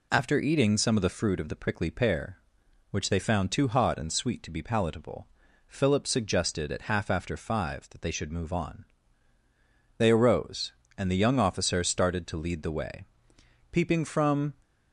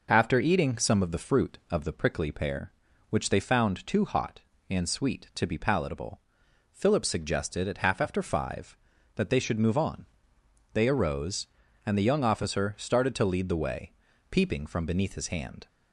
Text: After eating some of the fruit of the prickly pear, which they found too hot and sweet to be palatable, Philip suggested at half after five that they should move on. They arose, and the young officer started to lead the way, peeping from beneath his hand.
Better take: second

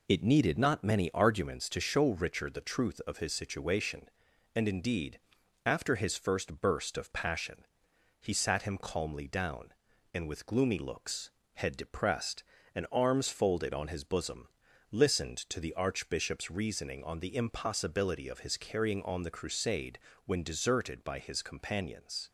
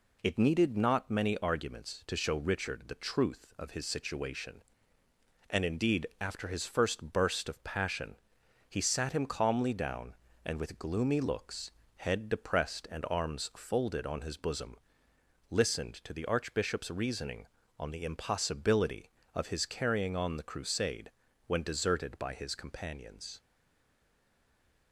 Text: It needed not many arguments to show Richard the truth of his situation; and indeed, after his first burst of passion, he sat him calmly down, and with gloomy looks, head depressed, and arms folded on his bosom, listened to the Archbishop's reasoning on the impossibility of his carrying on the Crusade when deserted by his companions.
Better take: first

